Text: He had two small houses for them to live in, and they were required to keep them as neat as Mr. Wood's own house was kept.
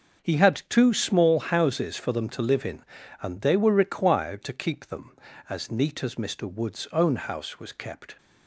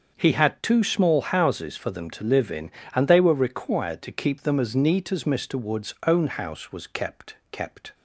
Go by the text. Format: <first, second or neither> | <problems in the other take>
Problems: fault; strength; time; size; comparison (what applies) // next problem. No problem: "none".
first | starts louder than the rest; until 1.1 s; 6.5 dB; also in the first // says "kept" twice; at 7.4 s